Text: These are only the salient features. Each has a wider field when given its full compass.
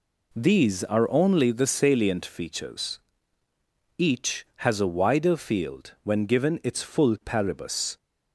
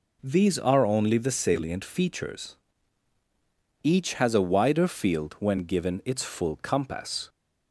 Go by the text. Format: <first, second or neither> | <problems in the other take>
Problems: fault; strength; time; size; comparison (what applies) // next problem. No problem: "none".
second | says "paribus" for "compass"; at 7.2 s